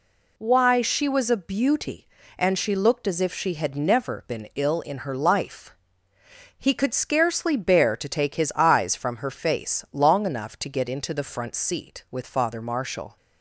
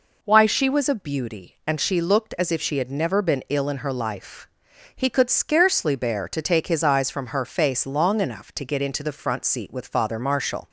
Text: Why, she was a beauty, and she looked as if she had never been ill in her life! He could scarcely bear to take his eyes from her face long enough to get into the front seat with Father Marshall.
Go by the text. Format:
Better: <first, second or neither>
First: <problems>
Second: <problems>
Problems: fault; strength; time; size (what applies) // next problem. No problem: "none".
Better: neither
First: none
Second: none